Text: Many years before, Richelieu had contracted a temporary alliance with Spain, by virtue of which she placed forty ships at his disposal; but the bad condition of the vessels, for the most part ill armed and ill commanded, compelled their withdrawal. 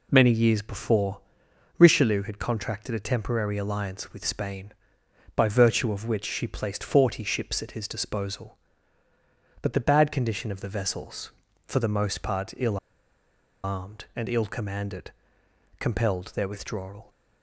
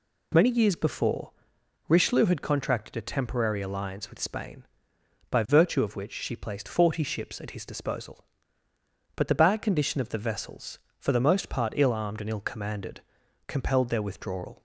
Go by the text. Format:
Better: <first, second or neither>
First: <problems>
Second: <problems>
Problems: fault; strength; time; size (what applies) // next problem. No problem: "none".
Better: second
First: pauses between "ill" and "armed"; noticeable; at 12.7 s; 0.86 s long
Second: none